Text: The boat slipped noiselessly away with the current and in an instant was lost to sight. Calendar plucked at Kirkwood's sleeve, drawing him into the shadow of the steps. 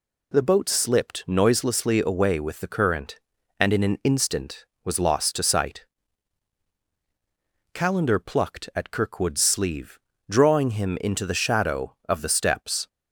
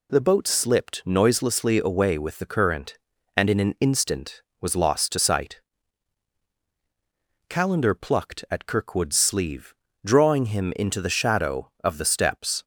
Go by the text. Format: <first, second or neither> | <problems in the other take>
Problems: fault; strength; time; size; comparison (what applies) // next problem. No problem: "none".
neither | none